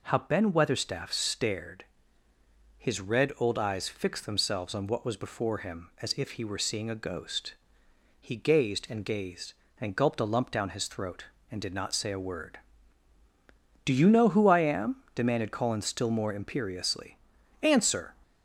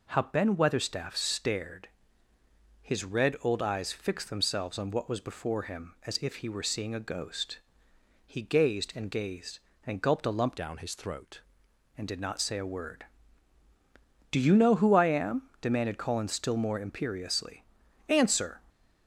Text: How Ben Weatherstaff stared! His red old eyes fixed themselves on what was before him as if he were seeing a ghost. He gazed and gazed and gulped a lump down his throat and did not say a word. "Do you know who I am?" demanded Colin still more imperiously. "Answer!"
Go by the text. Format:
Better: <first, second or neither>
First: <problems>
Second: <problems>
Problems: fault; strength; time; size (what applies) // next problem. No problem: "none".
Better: first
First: none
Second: changes voice from "down" to "throat"; from 10.5 to 11.4 s; 0.9 s long